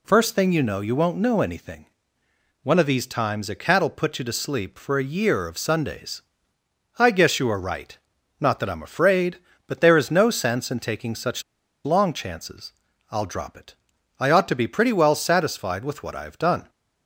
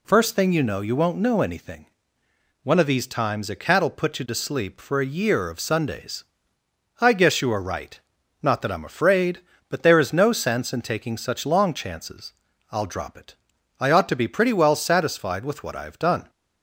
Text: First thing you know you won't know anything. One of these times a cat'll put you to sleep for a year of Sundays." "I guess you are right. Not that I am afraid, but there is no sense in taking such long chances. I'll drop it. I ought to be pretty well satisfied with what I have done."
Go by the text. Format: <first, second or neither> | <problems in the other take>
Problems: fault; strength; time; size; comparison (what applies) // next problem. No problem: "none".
second | pauses between "such" and "long"; at 11.4 s; 0.42 s long